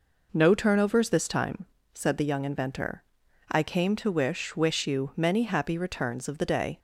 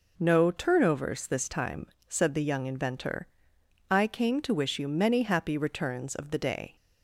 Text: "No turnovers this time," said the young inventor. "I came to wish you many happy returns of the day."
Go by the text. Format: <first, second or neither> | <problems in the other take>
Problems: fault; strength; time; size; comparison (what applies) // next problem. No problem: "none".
second | says "wish" twice; at 4.5 s